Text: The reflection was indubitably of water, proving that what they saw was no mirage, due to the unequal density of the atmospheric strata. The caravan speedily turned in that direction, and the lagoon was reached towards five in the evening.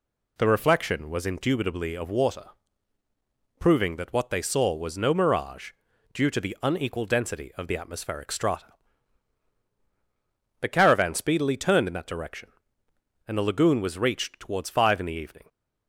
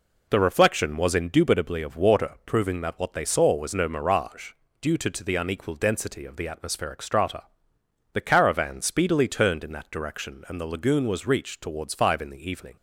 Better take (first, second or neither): first